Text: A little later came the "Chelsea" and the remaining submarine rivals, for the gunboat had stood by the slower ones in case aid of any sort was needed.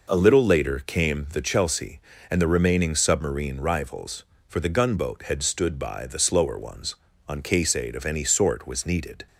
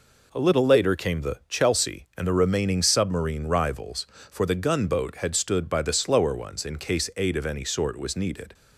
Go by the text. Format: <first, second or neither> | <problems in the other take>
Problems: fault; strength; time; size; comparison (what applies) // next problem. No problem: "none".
second | says "on" for "in"; at 7.2 s